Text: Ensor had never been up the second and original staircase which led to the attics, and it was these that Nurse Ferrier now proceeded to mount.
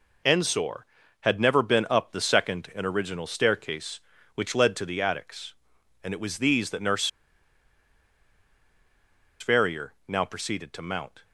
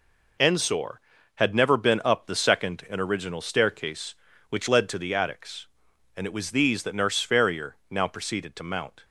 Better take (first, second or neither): second